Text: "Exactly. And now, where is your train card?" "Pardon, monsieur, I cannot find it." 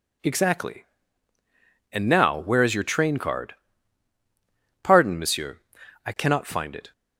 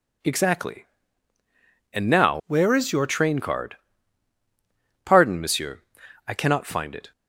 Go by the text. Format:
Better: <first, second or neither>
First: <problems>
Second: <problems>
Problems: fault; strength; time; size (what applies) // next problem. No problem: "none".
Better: first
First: none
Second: changes voice from "where" to "your"; from 2.4 to 3.0 s; 0.6 s long